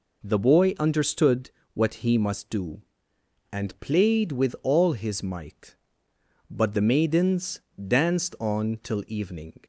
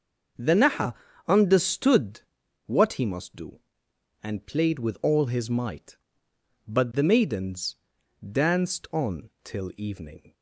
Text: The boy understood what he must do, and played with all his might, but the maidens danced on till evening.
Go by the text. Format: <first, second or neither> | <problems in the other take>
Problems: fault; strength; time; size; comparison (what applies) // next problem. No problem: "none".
first | starts louder than the rest; noticeable; until 1.7 s; 6 dB // says "naha" for "boy"; at 0.5 s // pauses between "understood" and "what"; noticeable; at 2.1 s; 0.46 s long; slight in the first // pauses between "maidens" and "danced"; noticeable; at 7.7 s; 0.58 s long; slight in the first